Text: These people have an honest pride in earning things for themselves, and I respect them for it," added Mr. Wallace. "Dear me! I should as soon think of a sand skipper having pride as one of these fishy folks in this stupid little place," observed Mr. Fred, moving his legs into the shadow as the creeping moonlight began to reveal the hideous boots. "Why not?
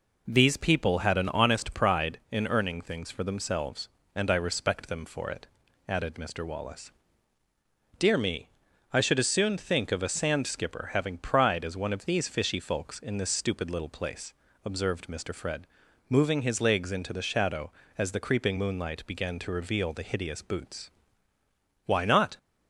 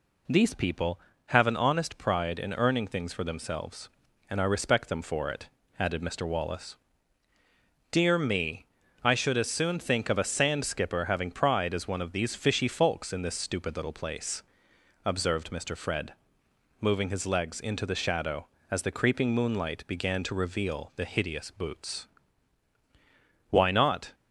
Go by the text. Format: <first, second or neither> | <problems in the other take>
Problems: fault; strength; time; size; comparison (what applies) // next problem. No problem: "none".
second | says "had" for "have"; at 0.9 s